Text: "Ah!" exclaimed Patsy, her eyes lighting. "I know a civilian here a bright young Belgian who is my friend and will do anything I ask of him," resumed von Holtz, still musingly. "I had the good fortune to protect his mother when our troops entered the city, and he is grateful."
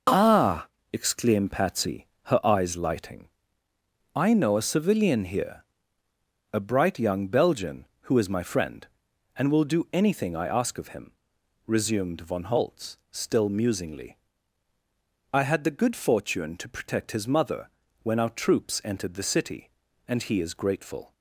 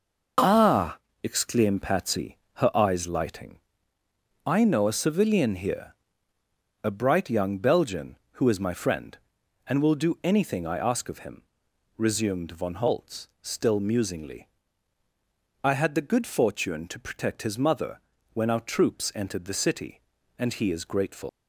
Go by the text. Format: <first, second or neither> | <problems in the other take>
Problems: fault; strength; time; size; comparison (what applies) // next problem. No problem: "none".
first | pauses between "here" and "a"; noticeable; at 5.9 s; 0.86 s long; noticeable in the first // pauses between "mother" and "when"; slight; at 17.9 s; 0.34 s long; slight in the first // leaves "grateful" unfinished; at 21.2 s; 135 ms